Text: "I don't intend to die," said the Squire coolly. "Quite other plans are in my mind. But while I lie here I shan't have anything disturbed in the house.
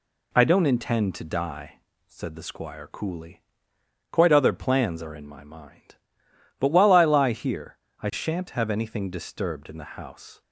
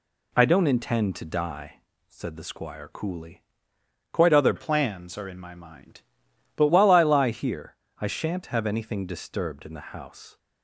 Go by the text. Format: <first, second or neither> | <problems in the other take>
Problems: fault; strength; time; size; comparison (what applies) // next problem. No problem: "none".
first | changes voice from "plans" to "But"; from 4.5 to 6.6 s; 2.1 s long // pauses between "here" and "I"; slight; at 7.7 s; 0.24 s long; slight in the first